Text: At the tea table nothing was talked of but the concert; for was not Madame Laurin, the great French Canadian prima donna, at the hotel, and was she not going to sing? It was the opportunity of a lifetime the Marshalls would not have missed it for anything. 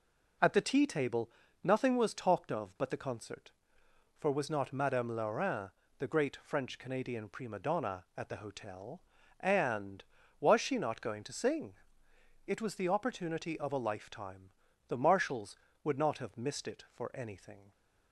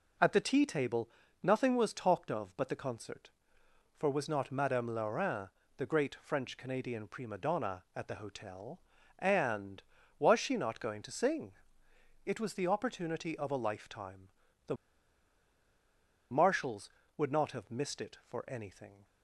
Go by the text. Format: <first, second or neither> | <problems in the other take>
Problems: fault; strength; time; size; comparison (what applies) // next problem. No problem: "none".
first | pauses between "table" and "nothing"; slight; at 1.0 s; 0.32 s long; slight in the first // pauses between "lifetime" and "the"; at 14.2 s; 0.38 s long; also in the first // pauses between "the" and "Marshalls"; strong; at 14.7 s; 1.5 s long